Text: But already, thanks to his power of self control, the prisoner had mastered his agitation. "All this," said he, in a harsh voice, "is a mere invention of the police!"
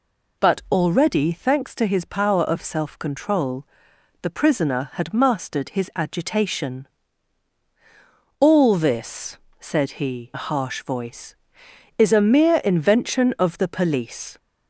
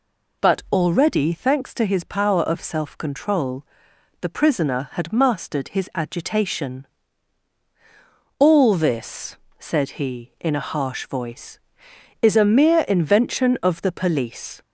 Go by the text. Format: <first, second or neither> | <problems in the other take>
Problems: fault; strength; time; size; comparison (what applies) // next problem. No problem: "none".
second | skips "in"; at 10.3 s